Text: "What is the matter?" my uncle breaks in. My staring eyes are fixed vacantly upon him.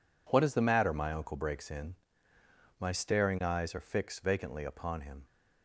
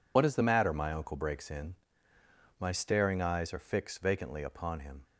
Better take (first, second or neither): first